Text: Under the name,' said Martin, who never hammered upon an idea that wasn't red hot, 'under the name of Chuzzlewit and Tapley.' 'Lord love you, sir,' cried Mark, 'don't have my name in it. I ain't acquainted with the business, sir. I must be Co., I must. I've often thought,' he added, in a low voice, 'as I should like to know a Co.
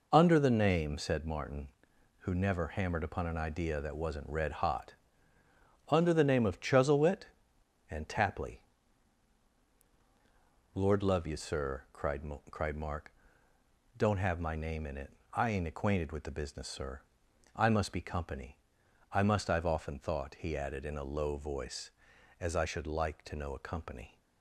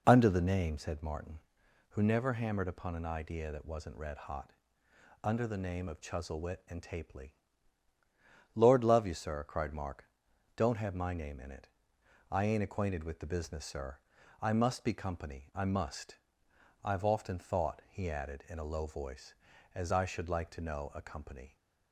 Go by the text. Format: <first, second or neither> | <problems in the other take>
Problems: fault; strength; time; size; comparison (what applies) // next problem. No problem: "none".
second | says "cried" twice; at 12.5 s